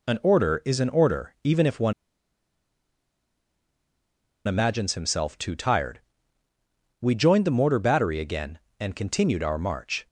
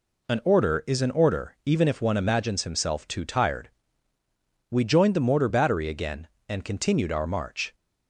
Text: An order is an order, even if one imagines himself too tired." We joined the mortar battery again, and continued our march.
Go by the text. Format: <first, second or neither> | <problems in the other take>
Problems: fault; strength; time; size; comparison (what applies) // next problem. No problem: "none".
second | pauses between "one" and "imagines"; strong; at 1.9 s; 2.5 s long